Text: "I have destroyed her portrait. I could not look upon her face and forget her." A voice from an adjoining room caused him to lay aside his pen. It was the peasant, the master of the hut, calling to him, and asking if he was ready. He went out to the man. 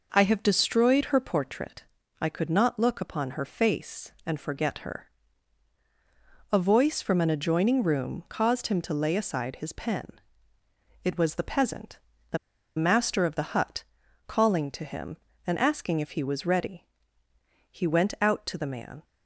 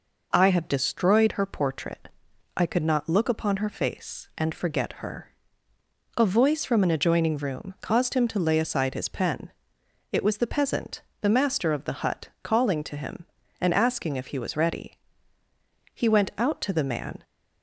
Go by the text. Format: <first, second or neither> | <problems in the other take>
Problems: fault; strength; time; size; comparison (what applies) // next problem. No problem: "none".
second | pauses between "the" and "master"; at 12.3 s; 0.39 s long